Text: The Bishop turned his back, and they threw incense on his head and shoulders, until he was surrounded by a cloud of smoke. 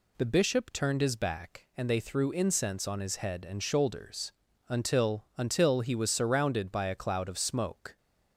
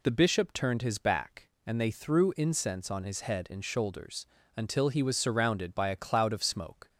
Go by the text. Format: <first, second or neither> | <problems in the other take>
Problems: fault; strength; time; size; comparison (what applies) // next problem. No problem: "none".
second | says "until" twice; at 5.3 s